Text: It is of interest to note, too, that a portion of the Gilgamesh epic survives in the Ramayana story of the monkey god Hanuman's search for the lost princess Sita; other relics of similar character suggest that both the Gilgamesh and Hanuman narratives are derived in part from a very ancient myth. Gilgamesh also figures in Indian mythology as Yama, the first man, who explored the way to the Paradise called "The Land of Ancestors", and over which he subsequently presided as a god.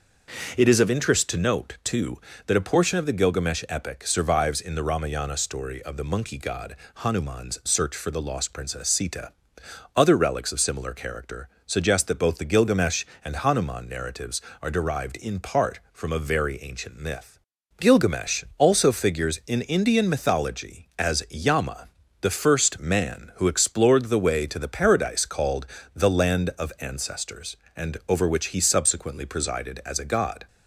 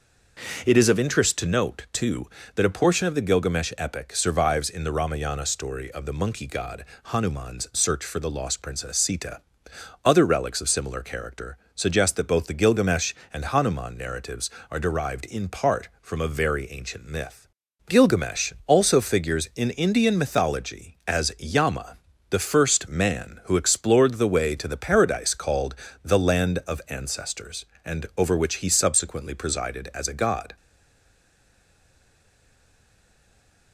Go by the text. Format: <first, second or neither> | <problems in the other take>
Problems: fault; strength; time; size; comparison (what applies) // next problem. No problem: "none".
first | pauses between "god" and "Hanuman's"; slight; at 6.8 s; 0.22 s long; slight in the first // pauses between "character" and "suggest"; slight; at 11.5 s; 0.16 s long; slight in the first // pauses between "called" and "The"; slight; at 25.7 s; 0.30 s long; slight in the first // stays silent after the last word; strong; from 30.5 s on; 3.2 s long